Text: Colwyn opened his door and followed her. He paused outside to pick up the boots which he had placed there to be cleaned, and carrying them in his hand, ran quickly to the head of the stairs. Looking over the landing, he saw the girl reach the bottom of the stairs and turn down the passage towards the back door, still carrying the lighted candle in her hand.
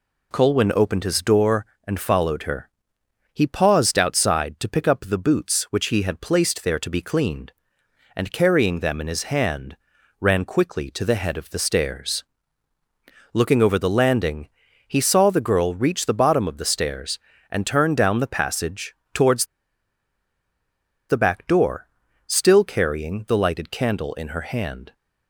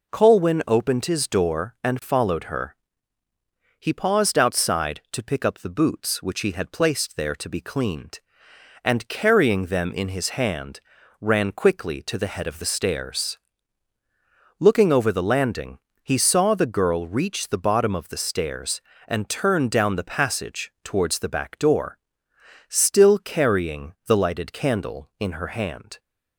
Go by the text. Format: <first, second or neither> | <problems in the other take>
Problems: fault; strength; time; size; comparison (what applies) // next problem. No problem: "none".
second | pauses between "passage" and "towards"; slight; at 18.9 s; 0.20 s long // pauses between "towards" and "the"; strong; at 19.4 s; 1.6 s long